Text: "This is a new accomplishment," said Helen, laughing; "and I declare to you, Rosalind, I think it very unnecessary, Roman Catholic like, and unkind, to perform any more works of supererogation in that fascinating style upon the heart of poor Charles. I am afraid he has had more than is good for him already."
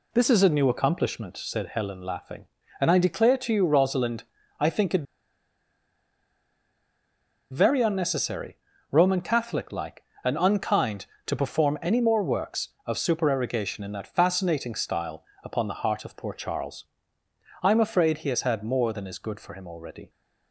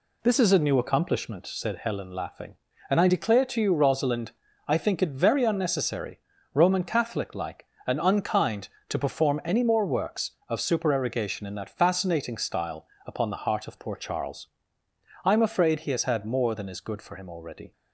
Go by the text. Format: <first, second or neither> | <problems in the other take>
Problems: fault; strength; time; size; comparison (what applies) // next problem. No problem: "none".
second | pauses between "it" and "very"; strong; at 5.0 s; 2.4 s long // pauses between "style" and "upon"; slight; at 15.2 s; 0.22 s long; slight in the second